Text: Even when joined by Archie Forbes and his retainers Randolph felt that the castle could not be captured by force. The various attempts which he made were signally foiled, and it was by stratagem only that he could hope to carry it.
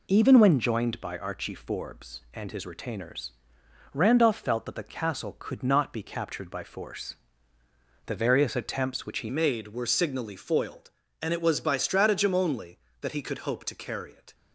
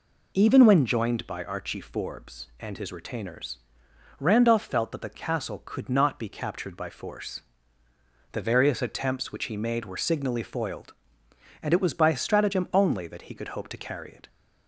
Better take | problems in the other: second | pauses between "retainers" and "Randolph"; noticeable; at 3.3 s; 0.62 s long; noticeable in the second // changes voice at "made"; from 9.2 s on; 5.1 s long

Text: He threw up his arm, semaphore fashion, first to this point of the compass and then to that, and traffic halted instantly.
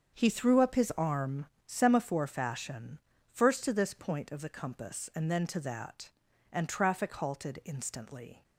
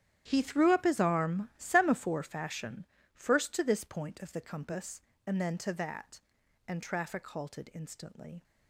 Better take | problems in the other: first | gets quieter; strong; throughout; 15 dB // starts louder than the rest; strong; until 1.2 s; 10.5 dB; also in the first

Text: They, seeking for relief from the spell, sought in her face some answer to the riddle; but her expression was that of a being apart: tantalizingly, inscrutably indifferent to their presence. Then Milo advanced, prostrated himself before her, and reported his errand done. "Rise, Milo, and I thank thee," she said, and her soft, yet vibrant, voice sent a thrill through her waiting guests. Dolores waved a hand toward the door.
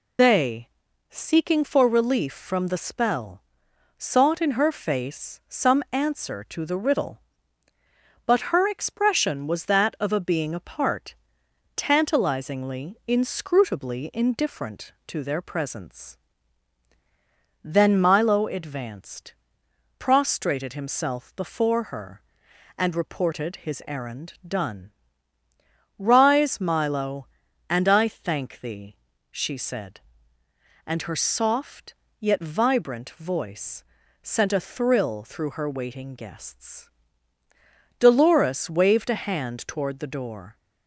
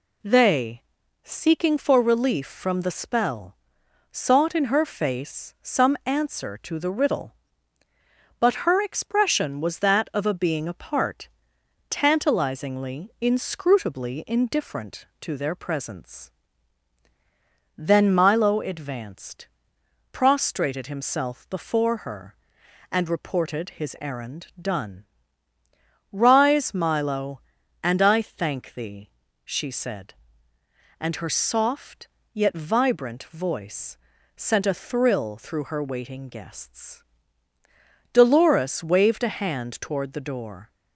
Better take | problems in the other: second | loses the start of "They"; at 0.1 s; 100 ms // pauses between "voice" and "sent"; at 33.8 s; 0.40 s long; also in the second

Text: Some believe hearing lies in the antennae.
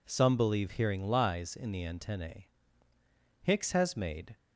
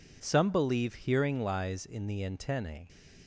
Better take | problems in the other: second | goes on to say "Hicks has made"; noticeable; from 3.4 s on; 0.96 s long

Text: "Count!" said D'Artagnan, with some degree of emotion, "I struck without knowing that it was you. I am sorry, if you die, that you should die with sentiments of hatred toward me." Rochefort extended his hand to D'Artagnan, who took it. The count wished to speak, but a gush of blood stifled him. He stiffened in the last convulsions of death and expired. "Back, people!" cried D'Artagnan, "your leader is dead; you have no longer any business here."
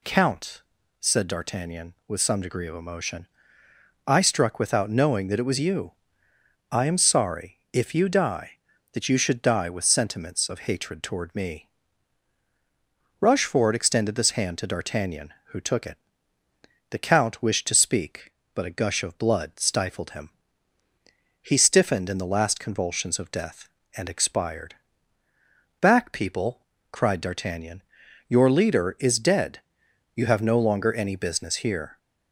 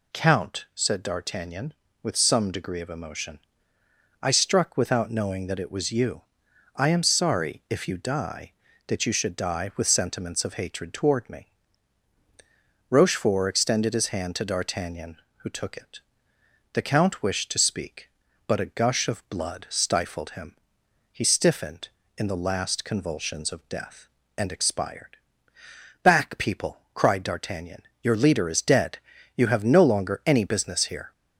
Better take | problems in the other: second | says "this" for "his"; at 14.1 s

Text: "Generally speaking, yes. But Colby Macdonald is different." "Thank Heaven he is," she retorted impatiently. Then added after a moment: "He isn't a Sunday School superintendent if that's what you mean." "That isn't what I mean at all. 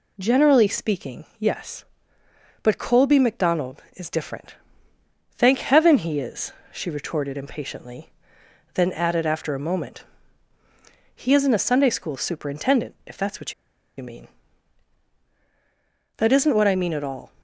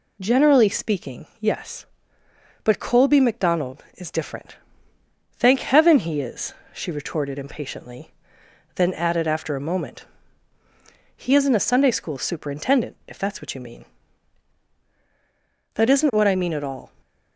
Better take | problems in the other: second | pauses between "what" and "you"; at 13.5 s; 0.44 s long

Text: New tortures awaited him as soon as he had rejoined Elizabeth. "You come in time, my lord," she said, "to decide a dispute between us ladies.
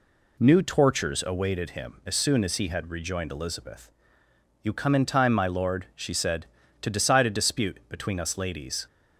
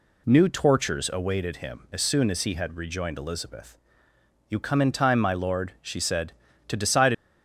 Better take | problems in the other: first | stops before "a dispute between us ladies"; at 7.1 s

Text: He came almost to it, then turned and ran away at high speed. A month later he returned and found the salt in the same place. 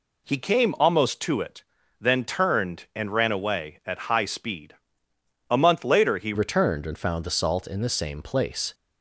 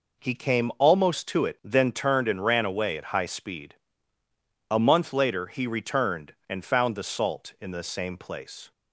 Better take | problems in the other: second | changes voice at "returned"; from 6.3 s on; 2.4 s long

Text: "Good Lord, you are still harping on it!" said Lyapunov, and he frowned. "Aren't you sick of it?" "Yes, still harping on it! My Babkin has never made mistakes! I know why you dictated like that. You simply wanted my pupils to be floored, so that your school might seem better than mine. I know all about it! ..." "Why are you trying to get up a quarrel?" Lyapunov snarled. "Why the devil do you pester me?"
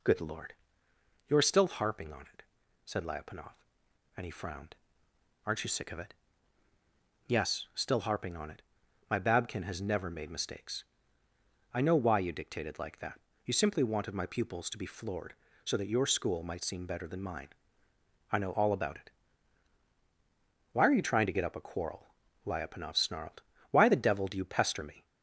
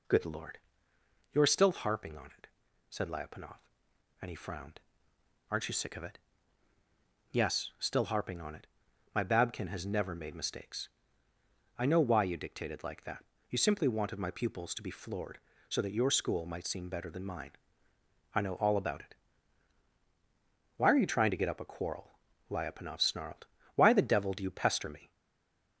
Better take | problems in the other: first | stays silent after the last word; slight; from 25.1 s on; 0.6 s long

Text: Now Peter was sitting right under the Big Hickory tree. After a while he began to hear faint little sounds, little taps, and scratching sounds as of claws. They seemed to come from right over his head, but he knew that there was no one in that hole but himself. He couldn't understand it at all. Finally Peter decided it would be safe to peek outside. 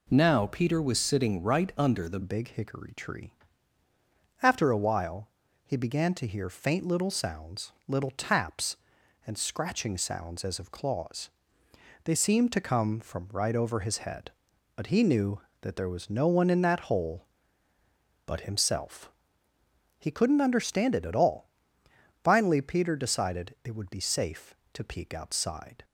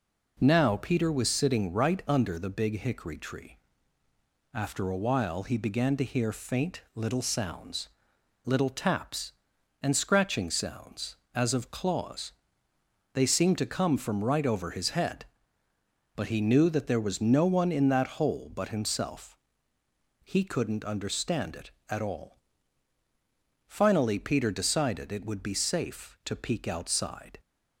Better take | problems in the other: second | changes voice at "Big"; from 2.2 s on; 23.6 s long // pauses between "while" and "he"; at 5.2 s; 0.38 s long

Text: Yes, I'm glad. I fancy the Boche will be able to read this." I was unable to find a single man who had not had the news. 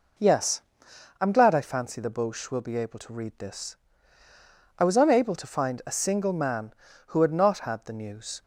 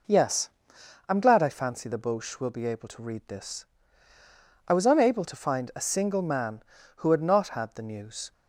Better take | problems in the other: neither | none

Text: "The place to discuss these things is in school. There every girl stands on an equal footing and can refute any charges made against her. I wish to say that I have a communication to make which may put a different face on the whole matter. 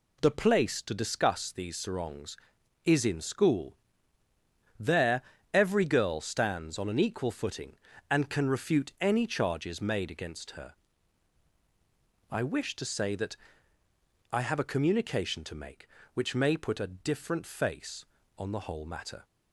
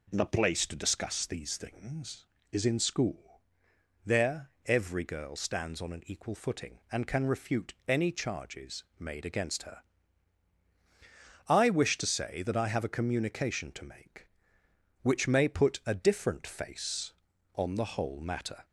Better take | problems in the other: second | says "sarongs" for "things"; at 1.7 s // pauses between "There" and "every"; slight; at 5.2 s; 0.32 s long; slight in the second // pauses between "that" and "I"; noticeable; at 13.3 s; 0.96 s long

